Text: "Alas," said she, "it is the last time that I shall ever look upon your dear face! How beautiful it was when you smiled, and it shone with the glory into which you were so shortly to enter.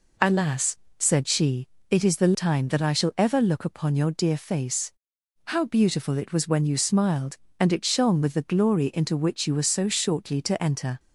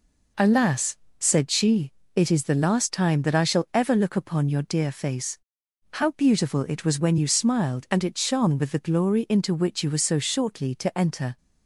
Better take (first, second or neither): second